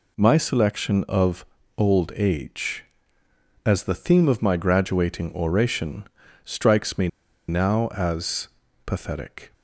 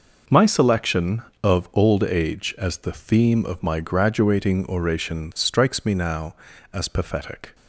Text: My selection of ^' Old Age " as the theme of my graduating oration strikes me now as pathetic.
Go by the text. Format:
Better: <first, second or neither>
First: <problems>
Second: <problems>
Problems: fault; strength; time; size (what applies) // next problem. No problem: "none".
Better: second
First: pauses between "oration" and "strikes"; at 6.0 s; 0.38 s long // pauses between "me" and "now"; at 7.0 s; 0.40 s long // pauses between "as" and "pathetic"; slight; at 8.4 s; 0.36 s long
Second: none